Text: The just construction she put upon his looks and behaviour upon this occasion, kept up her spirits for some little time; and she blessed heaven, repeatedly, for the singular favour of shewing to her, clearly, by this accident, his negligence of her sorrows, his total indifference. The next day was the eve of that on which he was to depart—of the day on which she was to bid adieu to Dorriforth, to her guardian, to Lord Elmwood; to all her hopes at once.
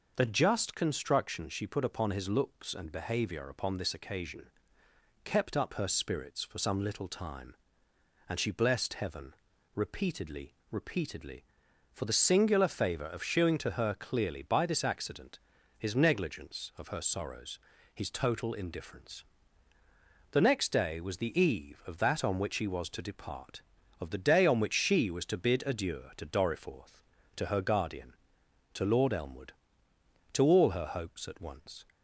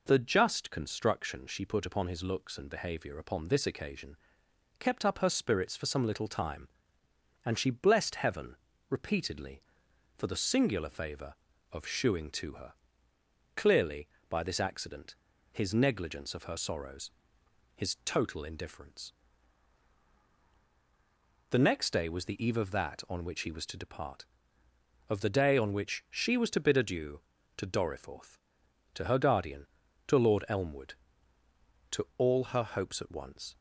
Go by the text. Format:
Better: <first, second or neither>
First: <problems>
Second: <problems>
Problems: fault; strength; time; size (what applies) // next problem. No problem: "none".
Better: second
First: says "repeatedly" twice; at 10.7 s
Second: none